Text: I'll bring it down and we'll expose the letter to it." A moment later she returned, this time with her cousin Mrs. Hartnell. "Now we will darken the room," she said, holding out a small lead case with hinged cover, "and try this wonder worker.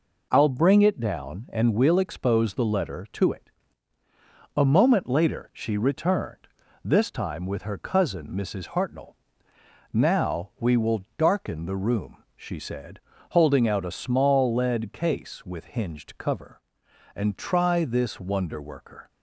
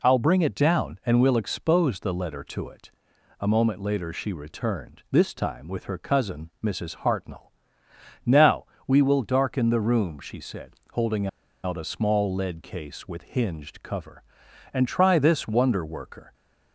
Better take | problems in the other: first | pauses between "Now" and "we"; slight; at 8.6 s; 0.22 s long // pauses between "holding" and "out"; at 11.2 s; 0.36 s long

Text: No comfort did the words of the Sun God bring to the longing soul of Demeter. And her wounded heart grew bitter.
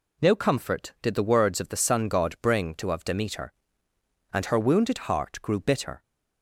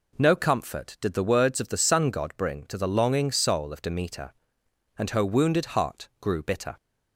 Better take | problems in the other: second | skips "the longing soul"; at 2.9 s

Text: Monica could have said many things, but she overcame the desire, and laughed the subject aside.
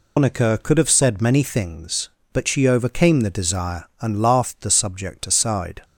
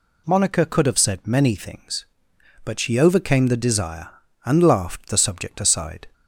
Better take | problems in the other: second | loses the start of "Monica"; at 0.1 s; 145 ms

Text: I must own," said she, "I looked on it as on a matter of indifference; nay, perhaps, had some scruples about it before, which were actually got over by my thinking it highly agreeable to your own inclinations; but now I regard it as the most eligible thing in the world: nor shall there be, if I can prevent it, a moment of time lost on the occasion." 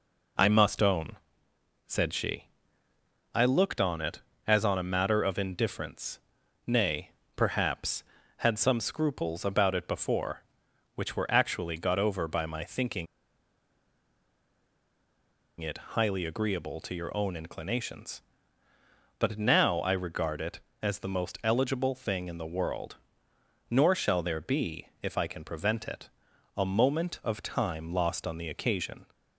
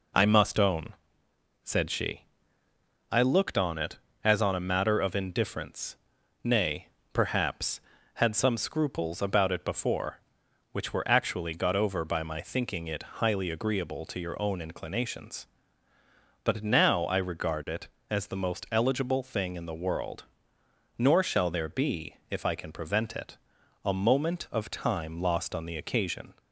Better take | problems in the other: second | pauses between "thinking" and "it"; strong; at 13.0 s; 2.5 s long // pauses between "it" and "highly"; slight; at 15.7 s; 0.16 s long; slight in the second

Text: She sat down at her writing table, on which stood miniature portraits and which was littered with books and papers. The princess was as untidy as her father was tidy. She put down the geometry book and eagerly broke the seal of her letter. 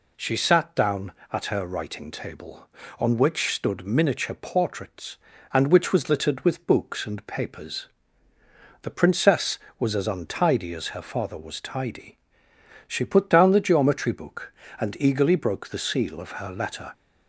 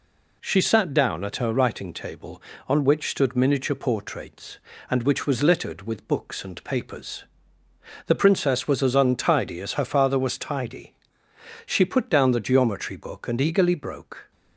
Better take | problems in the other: first | stops before "the seal of her letter"; at 14.3 s

